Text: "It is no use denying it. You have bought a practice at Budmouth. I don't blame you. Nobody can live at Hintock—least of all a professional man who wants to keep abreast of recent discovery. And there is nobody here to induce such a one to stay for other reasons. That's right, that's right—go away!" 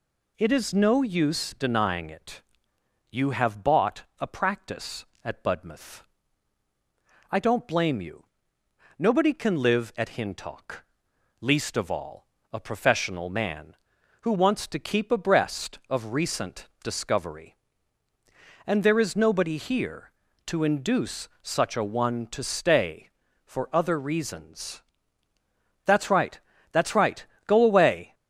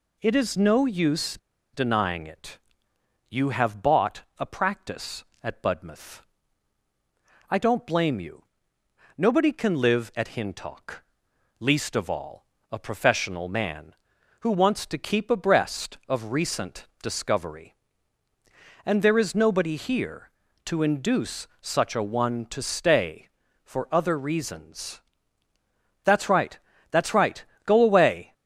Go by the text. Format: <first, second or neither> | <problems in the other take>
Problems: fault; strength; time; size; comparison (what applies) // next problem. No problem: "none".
first | pauses between "use" and "denying"; slight; at 1.3 s; 0.35 s long // pauses between "all" and "a"; slight; at 12.4 s; 0.24 s long; slight in the first